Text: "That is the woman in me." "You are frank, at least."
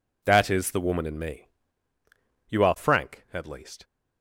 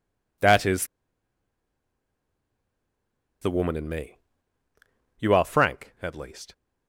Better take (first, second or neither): first